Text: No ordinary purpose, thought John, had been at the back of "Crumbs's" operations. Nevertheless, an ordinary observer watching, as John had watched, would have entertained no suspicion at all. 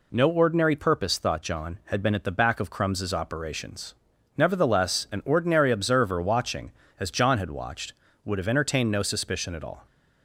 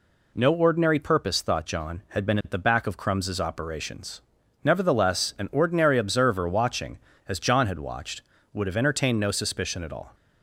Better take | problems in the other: neither | none

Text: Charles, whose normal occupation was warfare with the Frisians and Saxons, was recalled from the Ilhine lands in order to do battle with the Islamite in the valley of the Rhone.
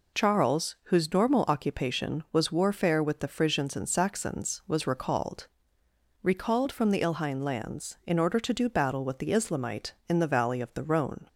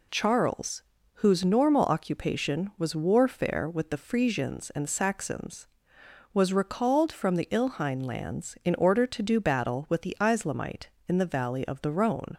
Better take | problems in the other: second | says "recalled" twice; at 6.2 s

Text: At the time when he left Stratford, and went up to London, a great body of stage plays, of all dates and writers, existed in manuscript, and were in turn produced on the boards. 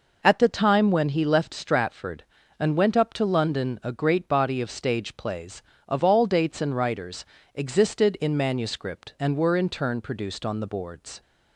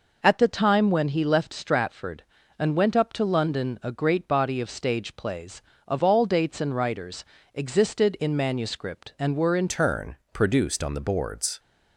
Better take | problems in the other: first | changes voice at "turn"; from 9.6 s on; 1.9 s long // pauses between "turn" and "produced"; slight; at 10.1 s; 0.16 s long

